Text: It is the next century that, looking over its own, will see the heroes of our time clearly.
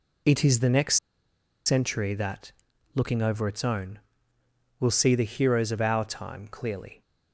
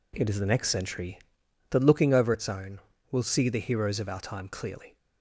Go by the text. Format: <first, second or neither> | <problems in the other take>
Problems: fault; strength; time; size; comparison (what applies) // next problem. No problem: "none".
second | pauses between "next" and "century"; noticeable; at 0.9 s; 0.69 s long